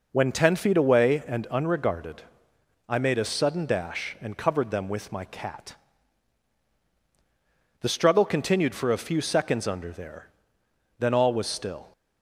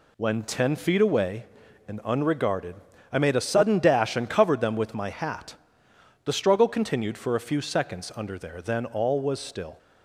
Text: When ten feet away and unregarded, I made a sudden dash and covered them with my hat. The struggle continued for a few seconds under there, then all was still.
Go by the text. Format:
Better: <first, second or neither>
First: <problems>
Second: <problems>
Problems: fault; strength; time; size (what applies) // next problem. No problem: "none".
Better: second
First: says "cat" for "hat"; at 5.2 s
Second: none